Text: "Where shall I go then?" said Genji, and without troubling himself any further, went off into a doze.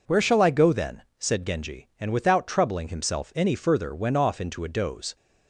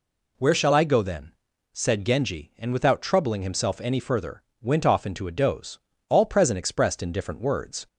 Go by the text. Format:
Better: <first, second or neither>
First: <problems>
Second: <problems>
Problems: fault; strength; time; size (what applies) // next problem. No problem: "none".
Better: first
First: none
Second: goes on to say "All present expressed in different words"; strong; from 6.0 s on; 1.7 s long